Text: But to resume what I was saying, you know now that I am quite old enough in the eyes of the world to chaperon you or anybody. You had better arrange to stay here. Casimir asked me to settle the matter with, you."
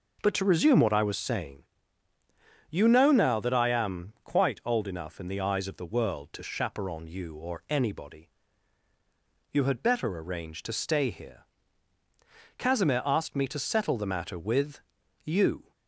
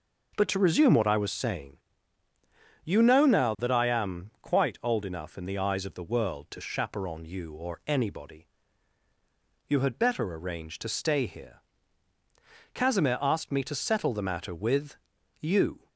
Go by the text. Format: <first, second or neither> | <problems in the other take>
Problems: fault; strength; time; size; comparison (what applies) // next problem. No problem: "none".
neither | none